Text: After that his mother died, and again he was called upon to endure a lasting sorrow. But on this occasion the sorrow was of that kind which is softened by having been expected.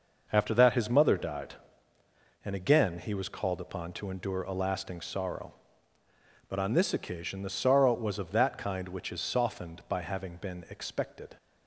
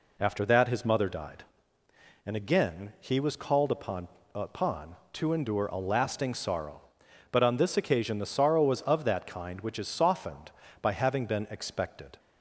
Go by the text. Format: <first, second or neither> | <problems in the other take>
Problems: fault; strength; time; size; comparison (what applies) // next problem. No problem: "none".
first | says "upon" twice; at 4.3 s